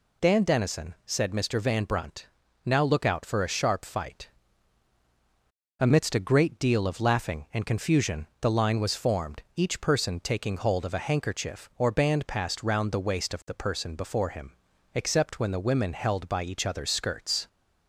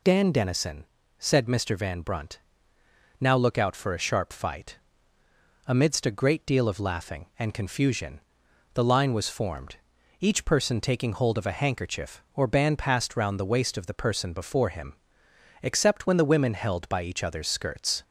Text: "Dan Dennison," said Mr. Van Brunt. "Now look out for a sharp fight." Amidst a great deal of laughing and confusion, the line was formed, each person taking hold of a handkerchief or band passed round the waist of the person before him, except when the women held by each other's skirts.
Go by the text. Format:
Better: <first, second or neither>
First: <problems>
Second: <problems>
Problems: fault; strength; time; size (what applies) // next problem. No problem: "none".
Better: neither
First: none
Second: none